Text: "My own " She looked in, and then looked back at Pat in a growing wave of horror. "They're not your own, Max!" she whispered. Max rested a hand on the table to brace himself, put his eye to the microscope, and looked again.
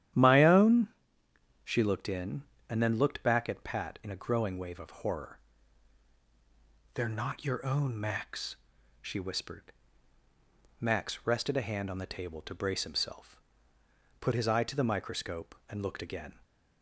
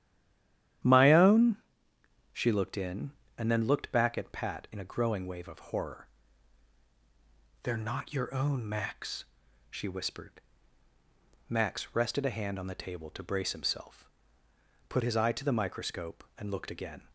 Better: first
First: starts louder than the rest; strong; until 1.5 s; 11 dB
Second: stays silent before the first word; slight; until 0.8 s; 0.8 s long // starts louder than the rest; strong; until 2.2 s; 11 dB

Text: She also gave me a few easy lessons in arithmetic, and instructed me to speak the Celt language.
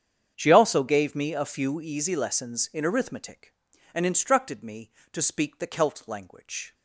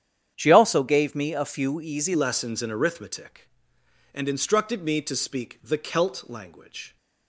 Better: first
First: starts louder than the rest; strong; until 1.3 s; 8 dB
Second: starts louder than the rest; strong; until 1.3 s; 9 dB // changes voice at "lessons"; from 2.1 s on; 4.8 s long

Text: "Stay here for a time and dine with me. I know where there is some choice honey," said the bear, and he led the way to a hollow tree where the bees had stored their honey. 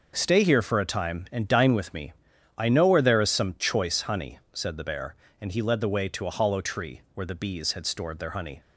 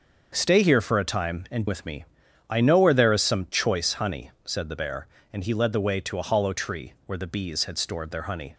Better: first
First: starts louder than the rest; noticeable; until 1.1 s; 6 dB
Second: starts louder than the rest; until 1.3 s; 6.5 dB // skips "dine"; at 1.6 s

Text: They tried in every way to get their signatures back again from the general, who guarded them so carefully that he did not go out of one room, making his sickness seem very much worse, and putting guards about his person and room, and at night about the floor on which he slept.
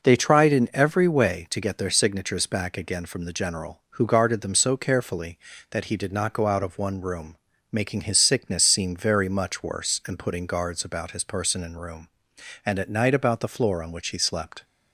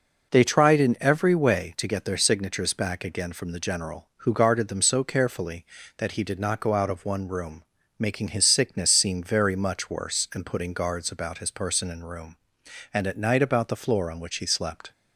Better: neither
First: none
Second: none

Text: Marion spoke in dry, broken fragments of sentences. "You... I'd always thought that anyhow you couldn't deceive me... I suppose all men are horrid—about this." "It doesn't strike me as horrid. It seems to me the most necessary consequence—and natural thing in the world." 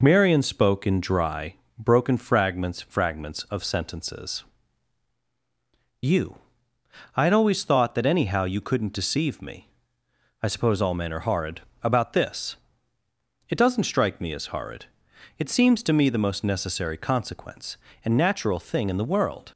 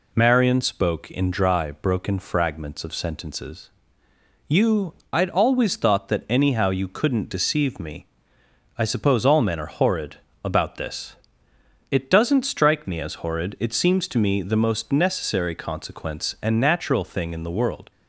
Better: second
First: says "fragments" twice; at 2.8 s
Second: none

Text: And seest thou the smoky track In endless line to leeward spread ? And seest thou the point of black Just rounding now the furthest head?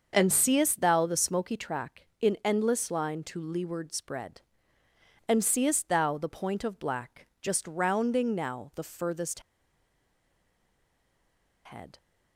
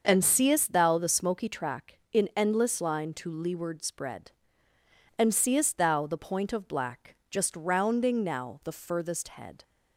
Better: second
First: starts louder than the rest; until 1.1 s; 6.5 dB // pauses between "black" and "Just"; slight; at 7.2 s; 0.16 s long // pauses between "furthest" and "head"; strong; at 9.3 s; 2.2 s long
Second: starts louder than the rest; until 1.1 s; 6.5 dB // pauses between "black" and "Just"; slight; at 7.1 s; 0.16 s long

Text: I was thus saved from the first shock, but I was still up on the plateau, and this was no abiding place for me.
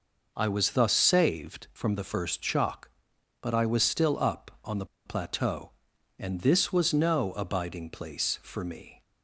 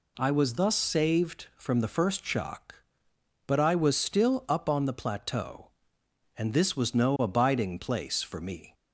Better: second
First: pauses between "the" and "plateau"; slight; at 4.8 s; 0.20 s long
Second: none

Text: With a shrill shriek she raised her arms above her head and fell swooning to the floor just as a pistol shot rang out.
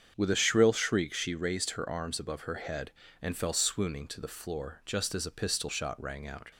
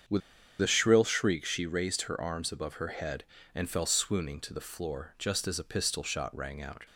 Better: first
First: starts louder than the rest; strong; until 1.1 s; 7.5 dB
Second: starts louder than the rest; strong; until 1.5 s; 7.5 dB // pauses between "With" and "a"; at 0.2 s; 0.40 s long

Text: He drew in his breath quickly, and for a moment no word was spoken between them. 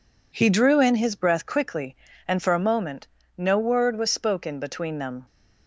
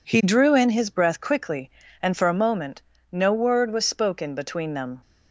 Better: neither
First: pauses between "moment" and "no"; slight; at 3.0 s; 0.30 s long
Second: pauses between "moment" and "no"; slight; at 2.8 s; 0.30 s long

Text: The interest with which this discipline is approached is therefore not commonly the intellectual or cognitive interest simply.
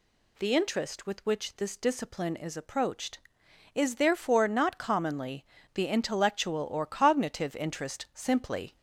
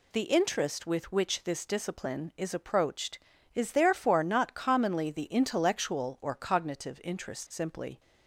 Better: second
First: gets louder; slight; throughout; 2.5 dB // pauses between "commonly" and "the"; slight; at 5.4 s; 0.30 s long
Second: none

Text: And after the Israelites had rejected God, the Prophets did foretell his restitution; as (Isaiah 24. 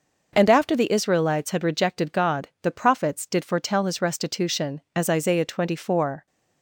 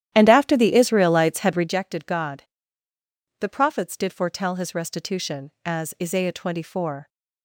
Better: first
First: none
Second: starts louder than the rest; strong; until 1.7 s; 11.5 dB

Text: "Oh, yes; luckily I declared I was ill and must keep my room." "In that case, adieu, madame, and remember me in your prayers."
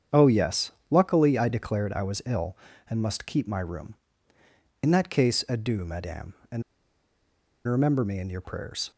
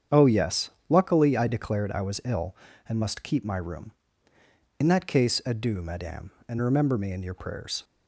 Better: second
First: starts louder than the rest; strong; until 1.3 s; 8 dB // pauses between "and" and "remember"; at 6.6 s; 1.0 s long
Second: starts louder than the rest; strong; until 1.2 s; 8 dB

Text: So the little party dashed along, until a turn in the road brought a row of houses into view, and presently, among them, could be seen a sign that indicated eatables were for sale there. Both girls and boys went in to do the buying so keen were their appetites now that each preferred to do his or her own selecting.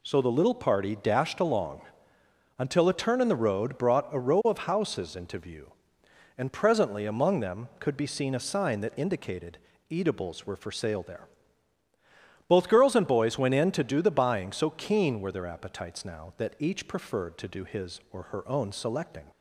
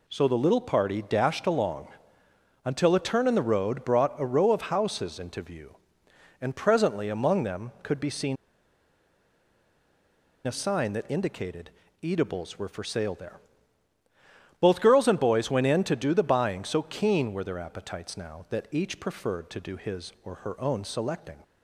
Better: first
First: pauses between "indicated" and "eatables"; slight; at 9.5 s; 0.32 s long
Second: pauses between "seen" and "a"; strong; at 8.3 s; 2.1 s long // pauses between "indicated" and "eatables"; slight; at 11.6 s; 0.32 s long

